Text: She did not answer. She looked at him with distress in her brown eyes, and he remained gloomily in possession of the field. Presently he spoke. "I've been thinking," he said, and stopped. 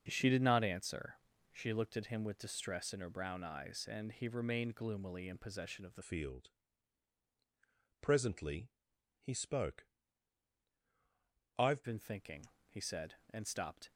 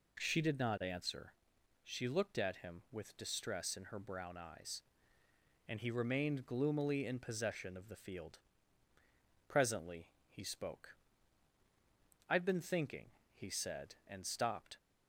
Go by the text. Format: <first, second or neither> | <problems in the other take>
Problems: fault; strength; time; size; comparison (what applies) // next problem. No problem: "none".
second | starts louder than the rest; until 1.0 s; 6.5 dB // changes voice from "field" to "I've"; from 6.0 to 11.8 s; 5.8 s long // pauses between "Presently" and "he"; noticeable; at 8.7 s; 0.48 s long; slight in the second